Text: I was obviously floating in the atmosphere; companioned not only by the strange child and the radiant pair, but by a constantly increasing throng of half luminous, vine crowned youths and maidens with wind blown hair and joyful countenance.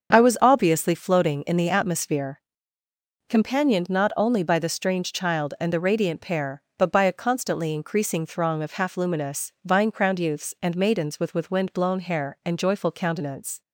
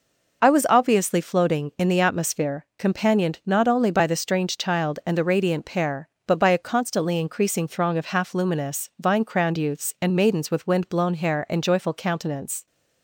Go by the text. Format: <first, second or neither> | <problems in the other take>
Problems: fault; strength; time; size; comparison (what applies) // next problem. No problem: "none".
second | starts louder than the rest; until 1.1 s; 7 dB // says "with" twice; at 11.3 s